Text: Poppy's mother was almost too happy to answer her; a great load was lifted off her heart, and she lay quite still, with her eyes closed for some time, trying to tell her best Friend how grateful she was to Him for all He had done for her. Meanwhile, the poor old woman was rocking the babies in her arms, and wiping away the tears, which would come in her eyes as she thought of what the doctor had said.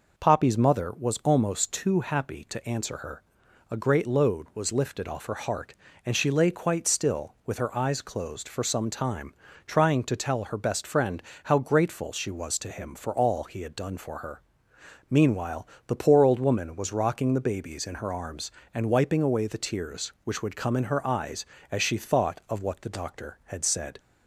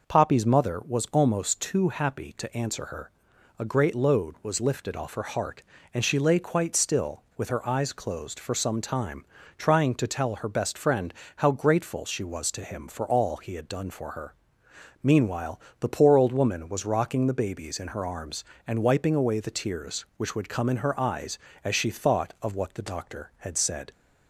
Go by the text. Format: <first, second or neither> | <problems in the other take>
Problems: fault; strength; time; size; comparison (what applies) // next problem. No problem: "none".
neither | pauses between "Friend" and "how"; slight; the same in both